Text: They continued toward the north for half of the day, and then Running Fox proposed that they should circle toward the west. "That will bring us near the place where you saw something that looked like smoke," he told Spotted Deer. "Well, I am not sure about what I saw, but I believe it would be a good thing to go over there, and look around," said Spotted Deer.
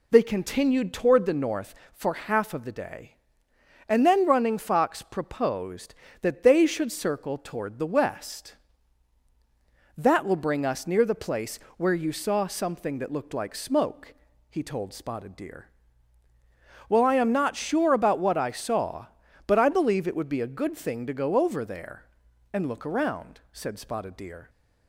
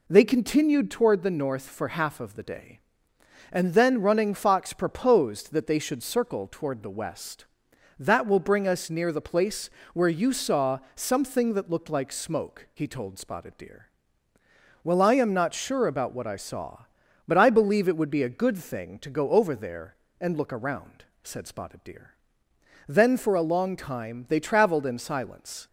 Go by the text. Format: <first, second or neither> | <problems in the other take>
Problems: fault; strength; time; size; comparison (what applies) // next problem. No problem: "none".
first | pauses between "place" and "where"; slight; at 9.7 s; 0.24 s long; slight in the first // goes on to say "Then for a long time they traveled in silence"; strong; from 22.8 s on; 2.8 s long